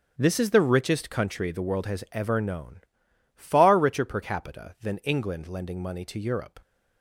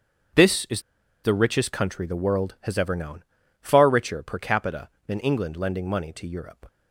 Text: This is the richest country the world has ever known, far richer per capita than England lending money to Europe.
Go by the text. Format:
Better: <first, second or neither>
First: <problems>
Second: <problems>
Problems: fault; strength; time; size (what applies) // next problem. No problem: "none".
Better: first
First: starts louder than the rest; strong; until 1.1 s; 8 dB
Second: starts louder than the rest; strong; until 1.8 s; 7.5 dB // pauses between "is" and "the"; at 0.7 s; 0.44 s long